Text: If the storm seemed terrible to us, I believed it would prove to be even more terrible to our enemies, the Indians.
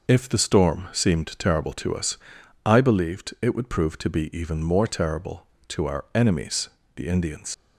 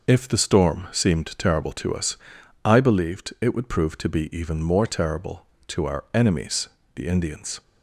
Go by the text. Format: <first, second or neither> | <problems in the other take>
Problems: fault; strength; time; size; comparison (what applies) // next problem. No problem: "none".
second | leaves "Indians" unfinished; at 7.5 s; 85 ms